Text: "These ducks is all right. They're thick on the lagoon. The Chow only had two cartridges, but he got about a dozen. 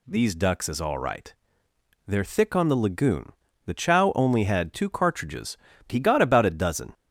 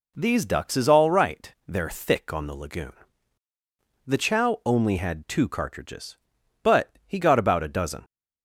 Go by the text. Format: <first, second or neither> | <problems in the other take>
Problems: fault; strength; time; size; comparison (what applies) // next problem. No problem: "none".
second | skips "but"; at 5.7 s